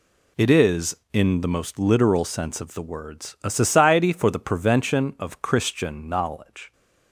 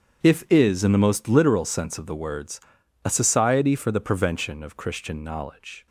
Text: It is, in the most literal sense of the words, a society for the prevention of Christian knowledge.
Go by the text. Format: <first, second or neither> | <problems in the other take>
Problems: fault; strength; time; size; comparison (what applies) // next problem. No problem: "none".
first | starts louder than the rest; strong; until 1.2 s; 8 dB // says "If" for "It"; at 0.2 s